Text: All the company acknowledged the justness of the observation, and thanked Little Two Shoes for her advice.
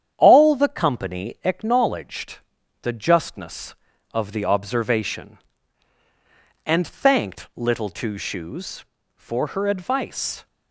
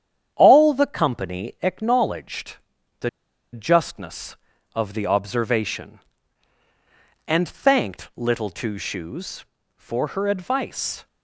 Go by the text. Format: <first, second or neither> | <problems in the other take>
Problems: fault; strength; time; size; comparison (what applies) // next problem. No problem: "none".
first | starts louder than the rest; strong; until 1.3 s; 9 dB; strong in the first // pauses between "acknowledged" and "the"; at 2.5 s; 0.44 s long; also in the first // pauses between "the" and "justness"; at 3.0 s; 0.45 s long